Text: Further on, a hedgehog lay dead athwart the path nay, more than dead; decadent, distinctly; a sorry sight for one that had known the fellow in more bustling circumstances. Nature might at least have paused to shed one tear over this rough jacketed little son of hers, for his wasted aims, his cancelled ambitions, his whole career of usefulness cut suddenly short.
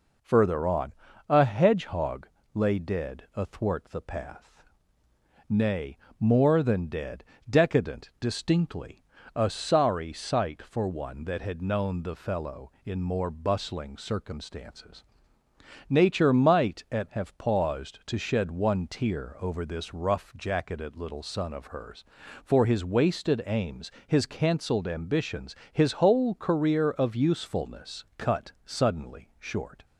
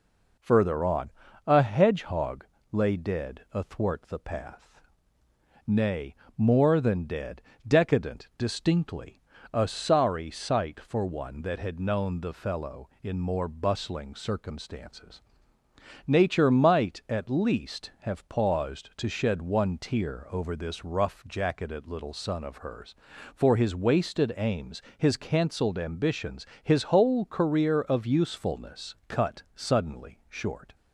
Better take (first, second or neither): second